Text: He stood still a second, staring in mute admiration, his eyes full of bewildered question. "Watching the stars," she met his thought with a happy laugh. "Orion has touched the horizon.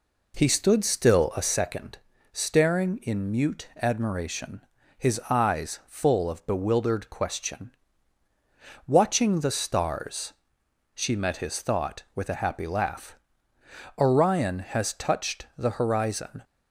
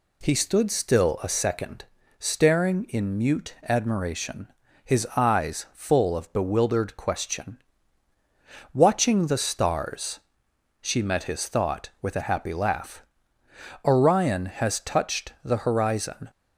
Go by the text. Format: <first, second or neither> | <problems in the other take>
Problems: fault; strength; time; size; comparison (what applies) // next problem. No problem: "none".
second | starts louder than the rest; until 1.7 s; 3.5 dB